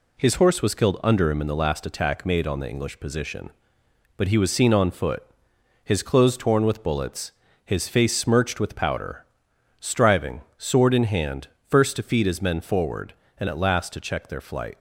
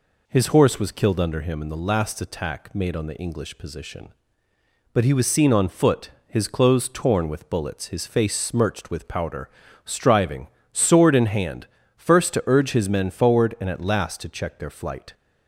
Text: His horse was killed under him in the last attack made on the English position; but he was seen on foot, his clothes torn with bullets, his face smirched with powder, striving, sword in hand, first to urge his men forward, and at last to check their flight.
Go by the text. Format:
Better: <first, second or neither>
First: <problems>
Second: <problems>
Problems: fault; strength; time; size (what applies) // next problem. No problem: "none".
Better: second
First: says "feed" for "urge"; at 12.0 s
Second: none